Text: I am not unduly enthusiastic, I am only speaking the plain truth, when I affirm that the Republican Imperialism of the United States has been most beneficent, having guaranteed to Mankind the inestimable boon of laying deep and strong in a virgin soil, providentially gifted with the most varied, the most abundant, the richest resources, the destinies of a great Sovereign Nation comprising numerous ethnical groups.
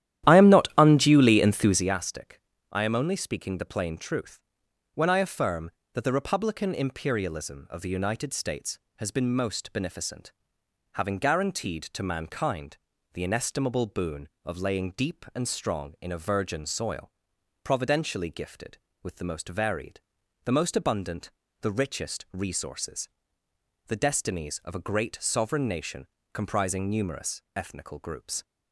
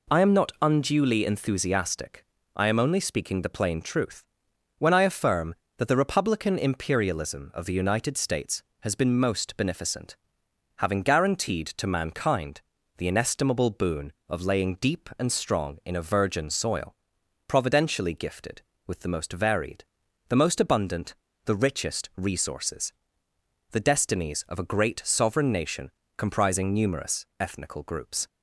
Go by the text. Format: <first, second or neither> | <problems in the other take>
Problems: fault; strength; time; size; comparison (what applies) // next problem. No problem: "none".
second | starts louder than the rest; strong; until 2.0 s; 12 dB // pauses between "Mankind" and "the"; slight; at 12.7 s; 0.34 s long; slight in the second // pauses between "Nation" and "comprising"; slight; at 26.0 s; 0.26 s long; slight in the second